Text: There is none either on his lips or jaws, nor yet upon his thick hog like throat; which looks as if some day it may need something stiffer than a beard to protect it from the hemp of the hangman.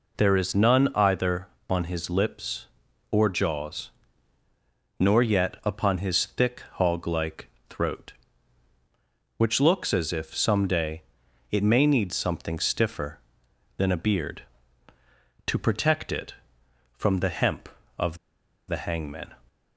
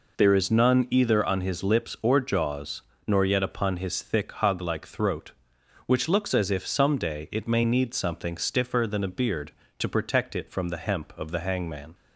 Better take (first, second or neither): second